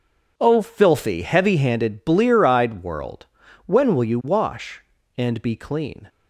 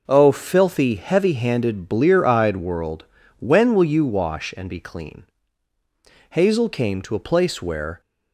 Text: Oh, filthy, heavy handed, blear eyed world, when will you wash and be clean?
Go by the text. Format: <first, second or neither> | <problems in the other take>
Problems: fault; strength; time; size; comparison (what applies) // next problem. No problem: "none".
first | goes on to say "Hazel came to a place where"; strong; from 6.3 s on; 1.7 s long